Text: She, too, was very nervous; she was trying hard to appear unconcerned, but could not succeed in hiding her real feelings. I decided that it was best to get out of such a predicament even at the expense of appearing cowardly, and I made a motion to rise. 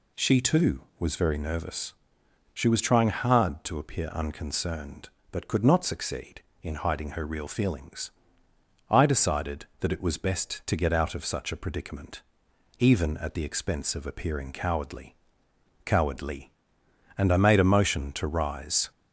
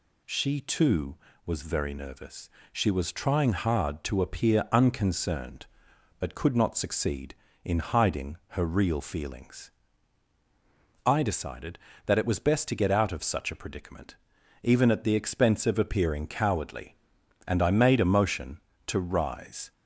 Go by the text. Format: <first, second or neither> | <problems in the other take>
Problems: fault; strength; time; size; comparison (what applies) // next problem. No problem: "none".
second | pauses between "predicament" and "even"; noticeable; at 12.2 s; 0.56 s long; noticeable in the second // says "cowardly" twice; at 15.8 s